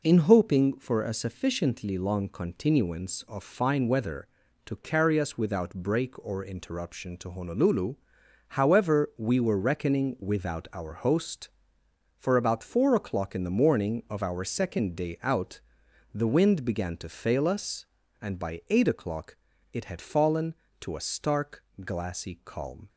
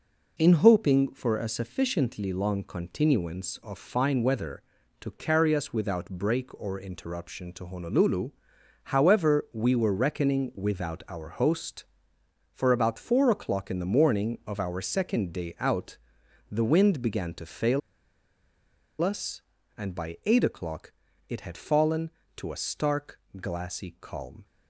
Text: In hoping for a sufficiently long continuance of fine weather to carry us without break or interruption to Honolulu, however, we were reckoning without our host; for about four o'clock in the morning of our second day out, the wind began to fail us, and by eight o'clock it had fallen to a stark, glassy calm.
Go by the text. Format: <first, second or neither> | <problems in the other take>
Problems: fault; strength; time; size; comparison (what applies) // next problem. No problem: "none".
first | pauses between "fail" and "us"; at 17.8 s; 1.2 s long // pauses between "o'clock" and "it"; at 20.9 s; 0.38 s long; also in the first